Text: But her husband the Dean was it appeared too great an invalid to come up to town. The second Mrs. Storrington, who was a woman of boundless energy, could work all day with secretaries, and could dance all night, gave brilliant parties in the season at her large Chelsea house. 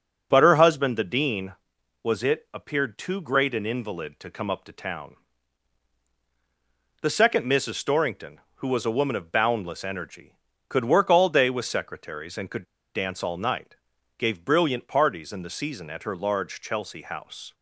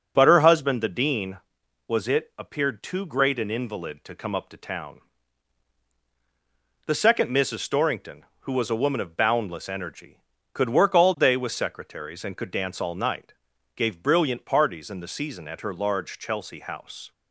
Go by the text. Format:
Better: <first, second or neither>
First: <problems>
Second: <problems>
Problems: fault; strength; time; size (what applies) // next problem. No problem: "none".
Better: second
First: starts louder than the rest; until 1.3 s; 6 dB // pauses between "could" and "dance"; slight; at 12.6 s; 0.31 s long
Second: starts louder than the rest; until 1.1 s; 6 dB